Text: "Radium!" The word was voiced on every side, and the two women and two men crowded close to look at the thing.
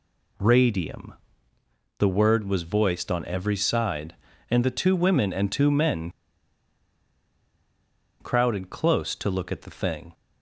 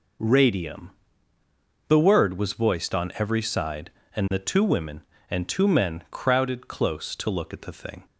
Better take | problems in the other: second | pauses between "men" and "crowded"; strong; at 6.1 s; 2.0 s long

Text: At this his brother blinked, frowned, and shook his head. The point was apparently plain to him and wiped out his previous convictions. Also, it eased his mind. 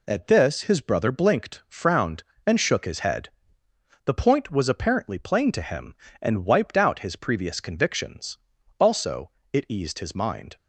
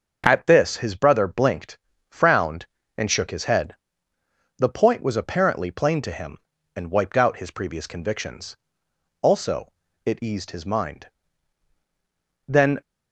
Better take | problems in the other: first | starts louder than the rest; until 1.2 s; 6 dB // goes on to say "Then"; slight; from 12.4 s on; 0.32 s long

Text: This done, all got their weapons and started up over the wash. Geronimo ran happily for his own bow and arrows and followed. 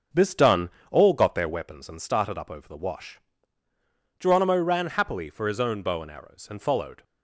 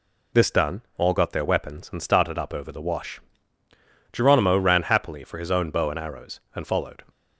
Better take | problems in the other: second | starts louder than the rest; until 1.7 s; 6 dB

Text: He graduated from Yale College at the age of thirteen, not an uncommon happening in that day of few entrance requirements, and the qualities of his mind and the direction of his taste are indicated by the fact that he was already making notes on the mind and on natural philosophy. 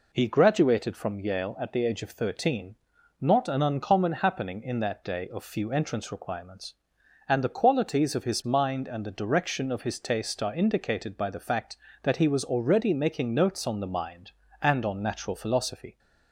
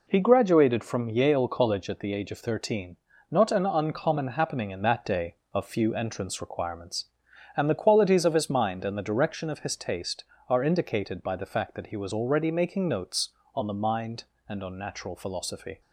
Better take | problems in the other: second | skips "College"; at 1.5 s

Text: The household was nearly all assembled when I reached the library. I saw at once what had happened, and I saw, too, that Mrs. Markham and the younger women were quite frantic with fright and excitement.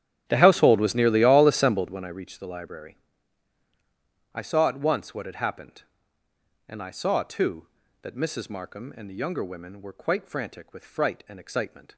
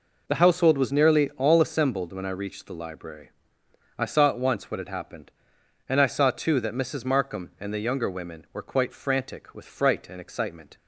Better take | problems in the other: second | starts louder than the rest; strong; until 2.0 s; 11.5 dB

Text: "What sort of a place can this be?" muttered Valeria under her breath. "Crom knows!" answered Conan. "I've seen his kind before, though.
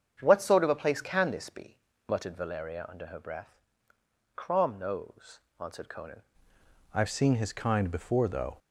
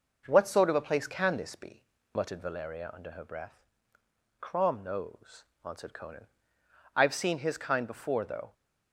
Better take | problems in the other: second | starts louder than the rest; strong; until 1.2 s; 7.5 dB // changes voice at "I've"; from 6.9 s on; 1.6 s long

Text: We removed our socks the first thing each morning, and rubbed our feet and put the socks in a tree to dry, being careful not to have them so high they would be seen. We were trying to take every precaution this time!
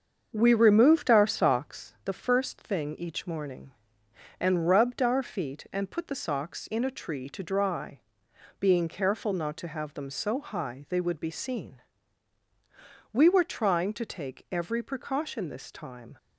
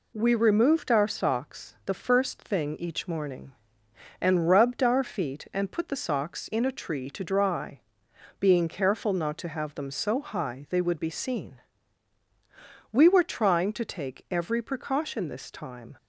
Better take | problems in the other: second | starts louder than the rest; until 1.9 s; 7 dB

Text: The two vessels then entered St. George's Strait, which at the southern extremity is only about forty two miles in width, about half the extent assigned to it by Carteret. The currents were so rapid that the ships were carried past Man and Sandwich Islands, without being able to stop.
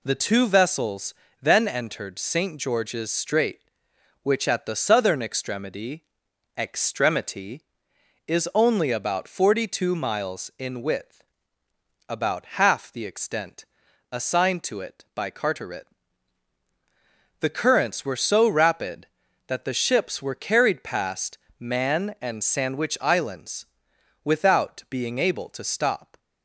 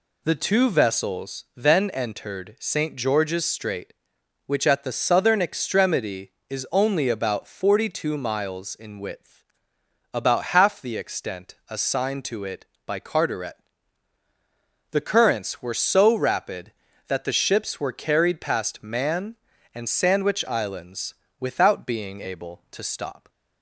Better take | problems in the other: second | pauses between "vessels" and "then"; slight; at 1.1 s; 0.26 s long // says "extremity" twice; at 6.5 s // pauses between "extent" and "assigned"; noticeable; at 13.6 s; 0.46 s long // pauses between "past" and "Man"; slight; at 21.3 s; 0.22 s long

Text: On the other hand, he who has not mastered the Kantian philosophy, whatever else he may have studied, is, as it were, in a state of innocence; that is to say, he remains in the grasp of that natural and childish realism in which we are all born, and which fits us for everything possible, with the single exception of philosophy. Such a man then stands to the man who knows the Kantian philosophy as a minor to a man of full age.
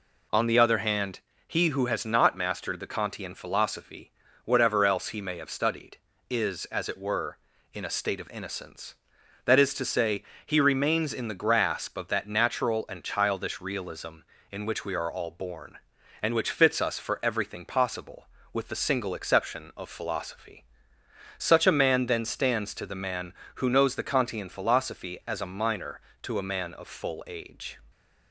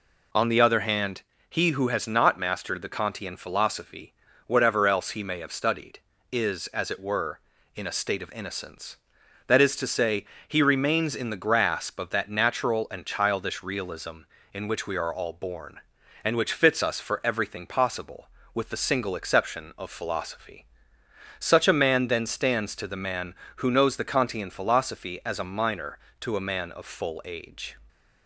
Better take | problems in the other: neither | none

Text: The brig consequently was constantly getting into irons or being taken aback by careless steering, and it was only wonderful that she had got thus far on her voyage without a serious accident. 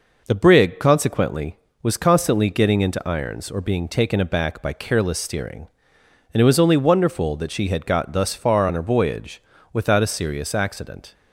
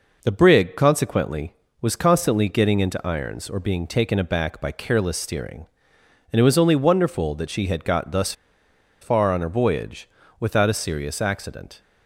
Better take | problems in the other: first | pauses between "thus" and "far"; noticeable; at 8.3 s; 0.69 s long // pauses between "voyage" and "without"; slight; at 10.0 s; 0.32 s long; slight in the first

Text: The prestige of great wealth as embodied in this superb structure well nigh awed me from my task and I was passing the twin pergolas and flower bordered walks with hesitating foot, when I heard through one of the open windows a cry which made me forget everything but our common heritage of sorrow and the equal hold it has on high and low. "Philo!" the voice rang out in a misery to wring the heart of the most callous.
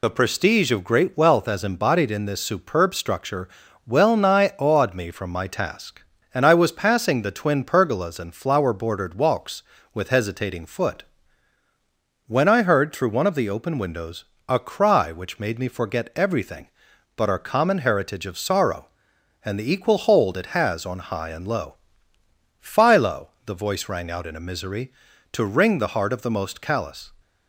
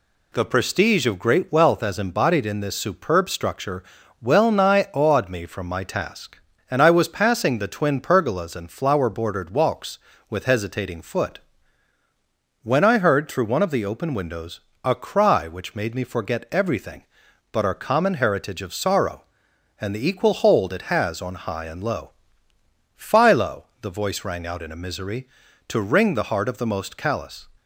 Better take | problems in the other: second | loses the start of "The"; at 0.0 s; 50 ms // pauses between "structure" and "well"; slight; at 3.4 s; 0.36 s long; slight in the second // pauses between "windows" and "a"; slight; at 14.2 s; 0.22 s long; slight in the second

